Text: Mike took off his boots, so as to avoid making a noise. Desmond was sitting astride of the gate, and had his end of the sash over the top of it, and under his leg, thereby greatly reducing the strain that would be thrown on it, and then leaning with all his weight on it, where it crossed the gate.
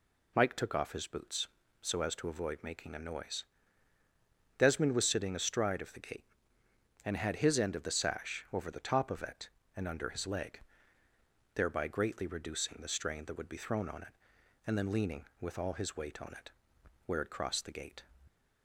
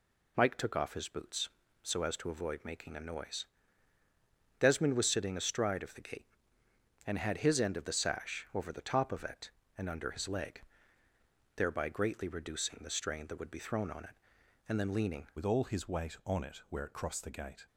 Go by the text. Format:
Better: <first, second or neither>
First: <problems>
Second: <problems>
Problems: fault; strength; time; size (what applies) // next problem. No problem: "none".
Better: first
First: none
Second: changes voice at "with"; from 15.3 s on; 2.3 s long